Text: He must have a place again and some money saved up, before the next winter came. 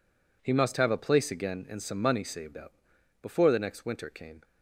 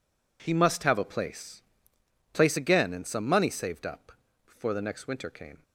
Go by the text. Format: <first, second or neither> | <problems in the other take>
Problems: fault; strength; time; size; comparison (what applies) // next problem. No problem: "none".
first | says "place" twice; at 2.3 s